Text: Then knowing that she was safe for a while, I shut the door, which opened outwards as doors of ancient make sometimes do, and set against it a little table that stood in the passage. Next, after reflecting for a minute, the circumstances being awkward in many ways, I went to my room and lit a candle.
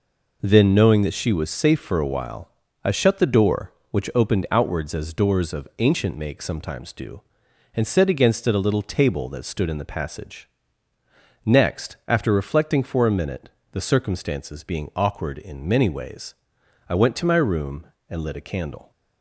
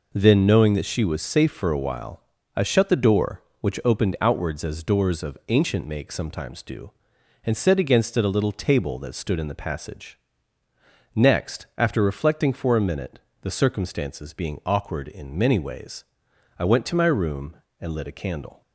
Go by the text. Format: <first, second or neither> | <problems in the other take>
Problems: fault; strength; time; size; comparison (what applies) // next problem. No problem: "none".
neither | none